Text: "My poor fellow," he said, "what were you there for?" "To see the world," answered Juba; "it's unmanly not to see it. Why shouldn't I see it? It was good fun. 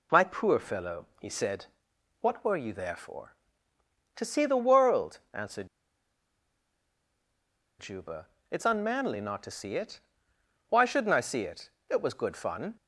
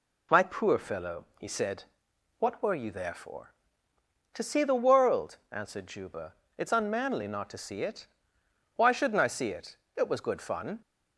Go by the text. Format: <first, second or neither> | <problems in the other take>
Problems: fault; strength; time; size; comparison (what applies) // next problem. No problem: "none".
second | pauses between "answered" and "Juba"; strong; at 5.6 s; 2.1 s long